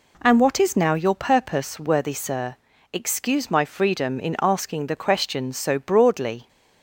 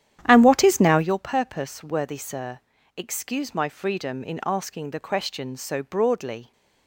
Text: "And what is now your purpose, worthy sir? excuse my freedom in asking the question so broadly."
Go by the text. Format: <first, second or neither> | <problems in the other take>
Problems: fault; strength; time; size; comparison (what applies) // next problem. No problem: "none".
first | starts louder than the rest; strong; until 1.2 s; 11 dB